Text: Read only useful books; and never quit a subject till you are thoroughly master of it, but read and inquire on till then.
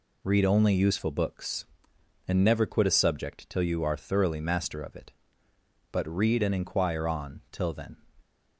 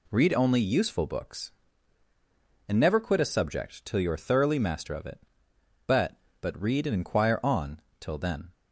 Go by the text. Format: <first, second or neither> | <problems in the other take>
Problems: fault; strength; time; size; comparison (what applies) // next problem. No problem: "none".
first | says "but" twice; at 6.4 s // pauses between "on" and "till"; slight; at 7.8 s; 0.18 s long